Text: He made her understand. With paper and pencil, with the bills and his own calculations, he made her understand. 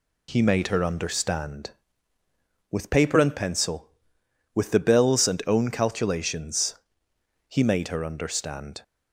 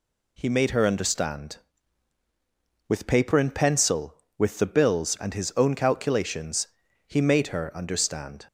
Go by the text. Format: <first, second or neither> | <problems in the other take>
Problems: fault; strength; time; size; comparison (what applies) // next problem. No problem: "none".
second | skips "his"; at 5.4 s